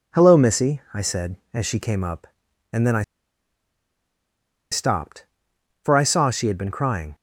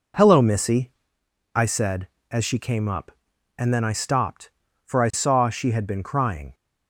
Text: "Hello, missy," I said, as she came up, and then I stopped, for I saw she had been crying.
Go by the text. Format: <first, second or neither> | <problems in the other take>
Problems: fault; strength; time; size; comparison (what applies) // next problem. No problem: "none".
second | pauses between "I" and "stopped"; strong; at 3.0 s; 1.6 s long